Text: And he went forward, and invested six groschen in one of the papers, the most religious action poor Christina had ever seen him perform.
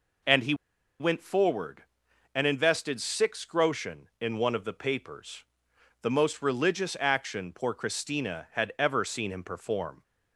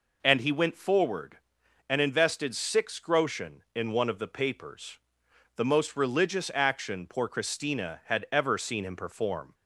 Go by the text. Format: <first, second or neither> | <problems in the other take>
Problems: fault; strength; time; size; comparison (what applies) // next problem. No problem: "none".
second | pauses between "he" and "went"; at 0.5 s; 0.45 s long